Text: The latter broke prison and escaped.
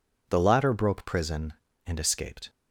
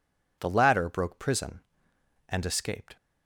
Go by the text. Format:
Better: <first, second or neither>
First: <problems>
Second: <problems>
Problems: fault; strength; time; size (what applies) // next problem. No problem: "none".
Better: neither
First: none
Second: none